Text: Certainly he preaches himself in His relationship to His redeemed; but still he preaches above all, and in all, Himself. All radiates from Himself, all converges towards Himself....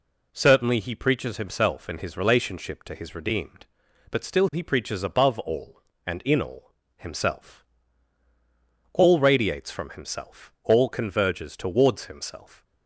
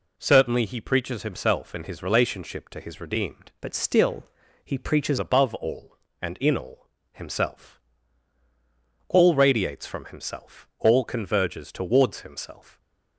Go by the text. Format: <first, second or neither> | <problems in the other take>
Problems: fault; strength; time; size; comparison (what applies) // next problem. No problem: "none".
first | changes voice from "but" to "preaches"; from 3.6 to 5.1 s; 1.5 s long // pauses between "still" and "he"; at 4.2 s; 0.40 s long